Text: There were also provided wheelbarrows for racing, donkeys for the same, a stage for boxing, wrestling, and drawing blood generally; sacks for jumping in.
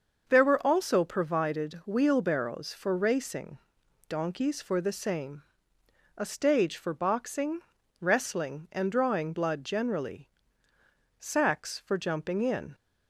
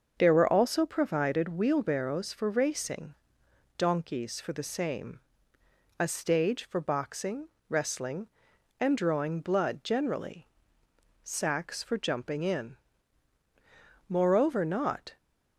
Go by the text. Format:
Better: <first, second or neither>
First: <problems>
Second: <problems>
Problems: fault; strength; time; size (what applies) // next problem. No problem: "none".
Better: first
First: starts louder than the rest; until 1.3 s; 6 dB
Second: starts louder than the rest; until 1.1 s; 6.5 dB // goes on to say "Moreover not"; noticeable; from 14.0 s on; 1.0 s long